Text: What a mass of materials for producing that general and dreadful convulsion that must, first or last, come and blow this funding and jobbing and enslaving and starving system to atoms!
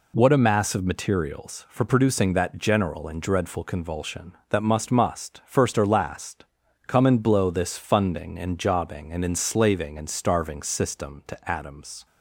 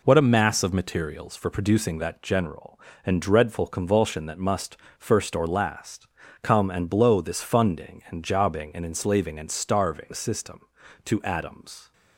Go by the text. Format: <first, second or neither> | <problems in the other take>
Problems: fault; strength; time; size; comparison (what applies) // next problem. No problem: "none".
second | says "must" twice; at 4.8 s